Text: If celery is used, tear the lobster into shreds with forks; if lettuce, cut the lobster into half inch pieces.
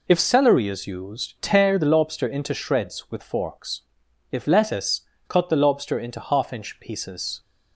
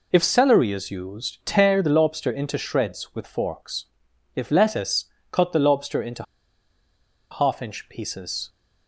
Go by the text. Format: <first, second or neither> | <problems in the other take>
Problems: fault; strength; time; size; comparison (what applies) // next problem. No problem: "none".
first | pauses between "into" and "half"; at 6.2 s; 1.0 s long